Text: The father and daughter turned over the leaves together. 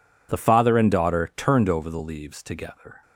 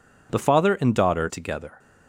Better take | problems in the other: first | skips "turned over the leaves"; at 1.2 s

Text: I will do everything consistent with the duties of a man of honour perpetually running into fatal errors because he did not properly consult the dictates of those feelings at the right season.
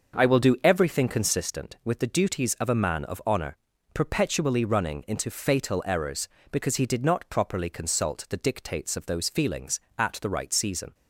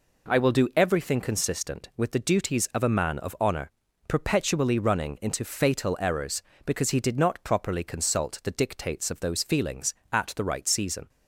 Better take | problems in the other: second | starts louder than the rest; until 1.5 s; 6.5 dB // pauses between "honour" and "perpetually"; at 3.5 s; 0.38 s long; also in the second

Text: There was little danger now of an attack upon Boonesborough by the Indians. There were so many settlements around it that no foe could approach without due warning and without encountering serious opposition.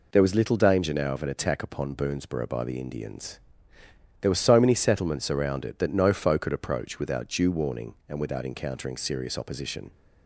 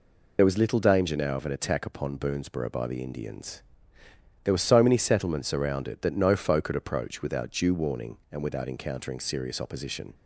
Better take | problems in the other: first | loses the start of "There"; at 0.3 s; 35 ms

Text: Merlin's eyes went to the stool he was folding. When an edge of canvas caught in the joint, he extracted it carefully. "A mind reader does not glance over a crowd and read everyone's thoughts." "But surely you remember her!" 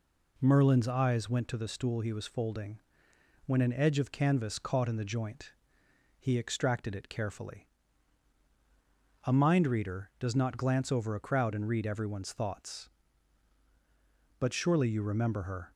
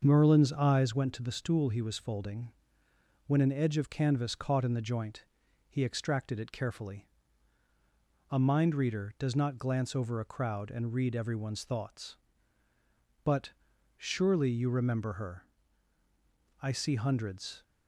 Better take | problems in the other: first | starts louder than the rest; until 1.0 s; 6.5 dB // pauses between "But" and "surely"; at 13.5 s; 0.42 s long // goes on to say "I see hundreds"; noticeable; from 16.6 s on; 1.0 s long

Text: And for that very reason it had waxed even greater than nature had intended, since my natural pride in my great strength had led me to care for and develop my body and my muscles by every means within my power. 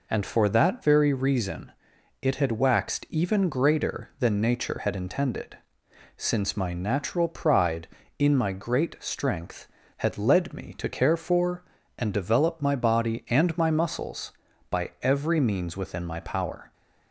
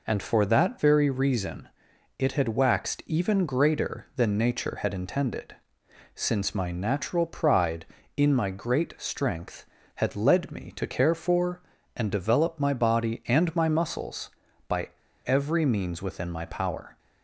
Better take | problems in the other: first | pauses between "reason" and "it"; noticeable; at 1.6 s; 0.50 s long; noticeable in the first // pauses between "by" and "every"; slight; at 14.8 s; 0.36 s long

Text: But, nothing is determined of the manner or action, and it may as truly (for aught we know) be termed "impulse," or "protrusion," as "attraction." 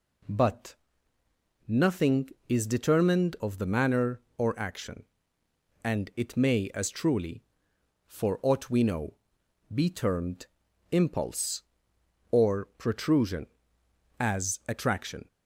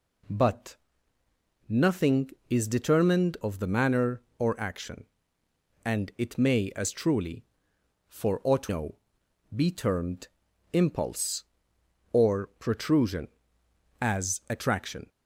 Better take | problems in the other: first | skips "we"; at 8.6 s // pauses between "termed" and "impulse"; noticeable; at 10.2 s; 0.46 s long; noticeable in the first

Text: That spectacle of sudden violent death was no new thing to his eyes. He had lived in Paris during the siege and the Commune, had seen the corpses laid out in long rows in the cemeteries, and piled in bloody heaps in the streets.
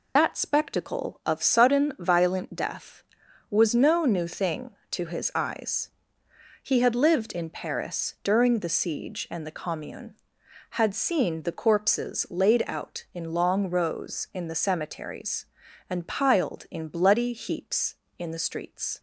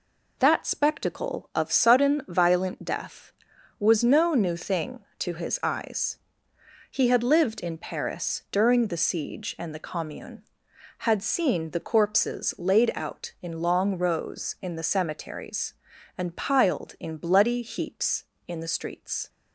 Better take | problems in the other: second | loses the start of "That"; at 0.1 s; 50 ms

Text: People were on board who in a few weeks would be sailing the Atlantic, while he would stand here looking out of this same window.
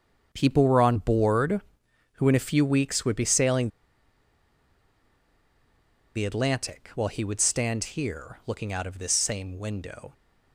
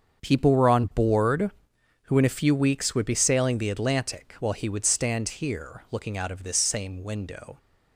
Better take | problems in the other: second | starts louder than the rest; until 1.3 s; 6.5 dB; also in the second // pauses between "sailing" and "the"; strong; at 3.6 s; 2.4 s long

